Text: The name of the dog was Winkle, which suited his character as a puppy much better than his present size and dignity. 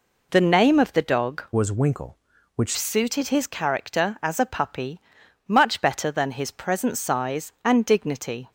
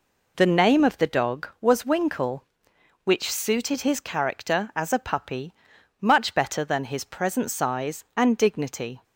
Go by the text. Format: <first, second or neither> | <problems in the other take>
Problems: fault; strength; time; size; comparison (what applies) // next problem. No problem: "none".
second | changes voice from "was" to "which"; from 1.5 to 2.7 s; 1.2 s long // pauses between "puppy" and "much"; noticeable; at 4.9 s; 0.48 s long; noticeable in the second